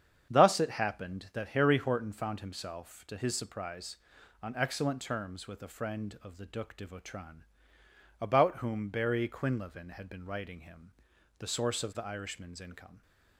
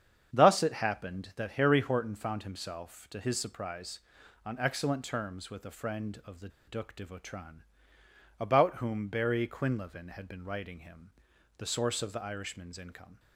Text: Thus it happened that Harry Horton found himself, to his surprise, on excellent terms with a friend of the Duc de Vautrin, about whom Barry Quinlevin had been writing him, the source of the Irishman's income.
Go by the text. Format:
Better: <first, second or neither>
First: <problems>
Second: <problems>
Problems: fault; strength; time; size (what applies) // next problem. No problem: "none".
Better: first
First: starts louder than the rest; strong; until 1.3 s; 8 dB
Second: starts louder than the rest; strong; until 1.3 s; 8 dB // pauses between "the" and "Duc"; slight; at 6.4 s; 0.18 s long